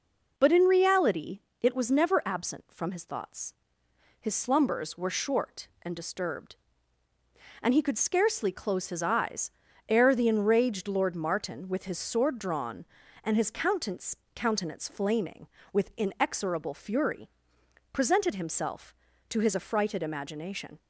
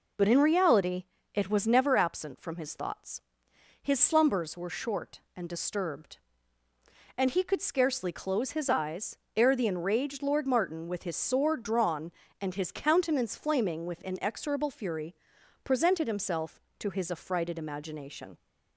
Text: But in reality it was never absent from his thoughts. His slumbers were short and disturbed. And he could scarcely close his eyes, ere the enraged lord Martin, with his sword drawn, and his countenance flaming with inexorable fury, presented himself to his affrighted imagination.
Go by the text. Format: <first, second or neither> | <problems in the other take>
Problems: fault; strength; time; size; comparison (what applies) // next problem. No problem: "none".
second | pauses between "reality" and "it"; slight; at 1.4 s; 0.22 s long; slight in the second // says "countenance" twice; at 14.3 s